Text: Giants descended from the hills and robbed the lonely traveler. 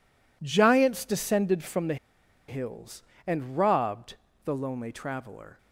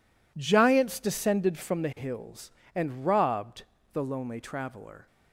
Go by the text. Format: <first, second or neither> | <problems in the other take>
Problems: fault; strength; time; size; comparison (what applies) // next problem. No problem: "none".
second | pauses between "the" and "hills"; noticeable; at 1.9 s; 0.52 s long // pauses between "robbed" and "the"; slight; at 4.1 s; 0.30 s long; slight in the second